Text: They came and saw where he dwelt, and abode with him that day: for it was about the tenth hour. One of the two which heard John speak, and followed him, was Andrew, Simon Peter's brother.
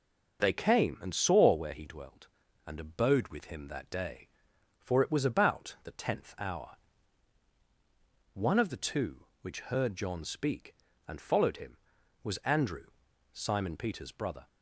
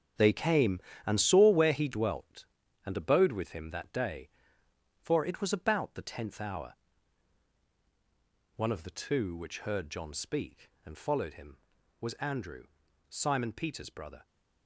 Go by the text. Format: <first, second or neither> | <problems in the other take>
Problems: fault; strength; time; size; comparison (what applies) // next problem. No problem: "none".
first | gets quieter; strong; throughout; 10.5 dB